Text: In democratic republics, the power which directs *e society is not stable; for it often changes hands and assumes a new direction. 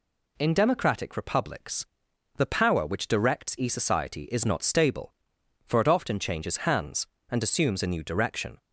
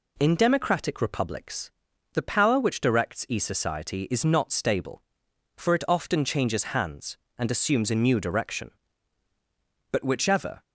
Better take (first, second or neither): first